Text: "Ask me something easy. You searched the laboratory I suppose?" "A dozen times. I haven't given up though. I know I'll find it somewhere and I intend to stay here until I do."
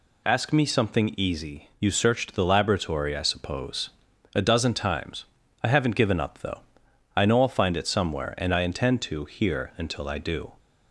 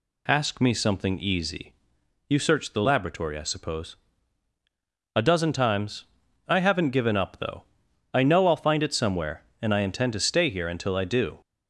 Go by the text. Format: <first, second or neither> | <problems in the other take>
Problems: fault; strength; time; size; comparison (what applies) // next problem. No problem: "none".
second | skips "stay"; at 9.2 s